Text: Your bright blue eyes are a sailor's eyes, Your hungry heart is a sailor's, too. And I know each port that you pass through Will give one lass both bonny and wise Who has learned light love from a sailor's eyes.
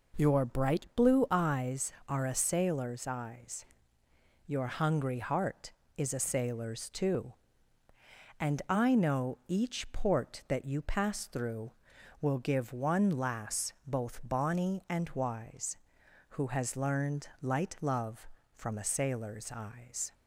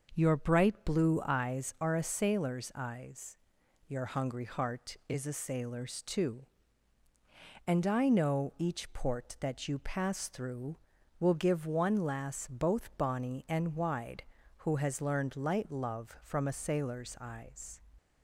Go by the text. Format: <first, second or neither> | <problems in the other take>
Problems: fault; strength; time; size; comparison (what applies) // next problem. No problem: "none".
first | says "wide" for "wise"; at 13.7 s